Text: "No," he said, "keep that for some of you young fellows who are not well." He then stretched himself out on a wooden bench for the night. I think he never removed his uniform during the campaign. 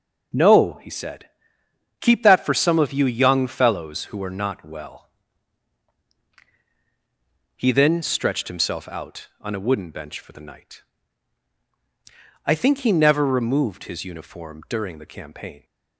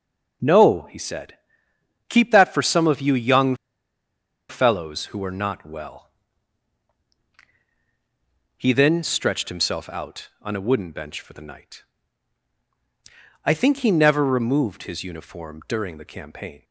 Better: first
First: none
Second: pauses between "young" and "fellows"; noticeable; at 3.5 s; 0.94 s long

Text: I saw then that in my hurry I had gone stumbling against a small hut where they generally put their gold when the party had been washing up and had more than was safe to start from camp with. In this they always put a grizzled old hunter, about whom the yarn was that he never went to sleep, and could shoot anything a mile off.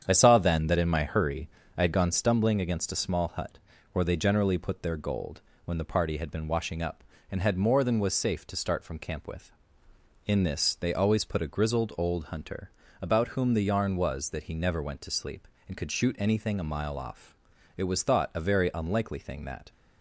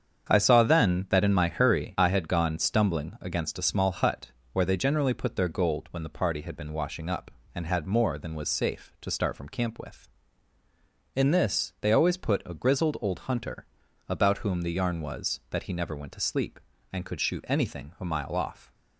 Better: second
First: starts louder than the rest; strong; until 1.0 s; 8.5 dB // pauses between "hurry" and "I"; slight; at 1.4 s; 0.28 s long // pauses between "hut" and "where"; slight; at 3.5 s; 0.34 s long // pauses between "gold" and "when"; slight; at 5.4 s; 0.24 s long // goes on to say "It was thought a very unlikely thing that"; strong; from 17.7 s on; 1.9 s long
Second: starts louder than the rest; strong; until 1.3 s; 7.5 dB // pauses between "hut" and "where"; slight; at 4.3 s; 0.20 s long

